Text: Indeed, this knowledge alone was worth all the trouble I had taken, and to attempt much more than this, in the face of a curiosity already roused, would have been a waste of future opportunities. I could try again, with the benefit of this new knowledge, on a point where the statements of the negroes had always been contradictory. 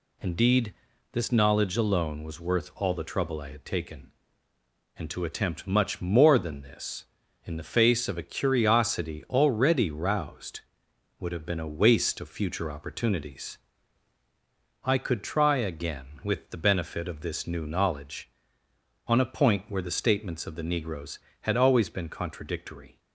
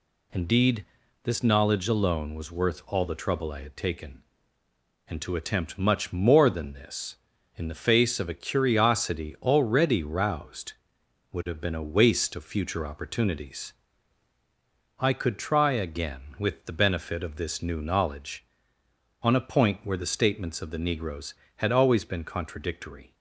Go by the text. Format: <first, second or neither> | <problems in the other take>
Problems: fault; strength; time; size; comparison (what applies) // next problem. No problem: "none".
neither | none